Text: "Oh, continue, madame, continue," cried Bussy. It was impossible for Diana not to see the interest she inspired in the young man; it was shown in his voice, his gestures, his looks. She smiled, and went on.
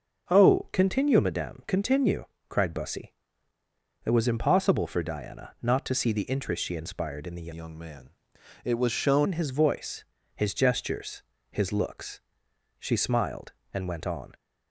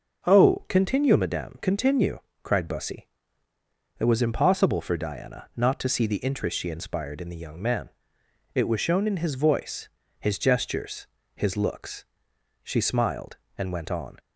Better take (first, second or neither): second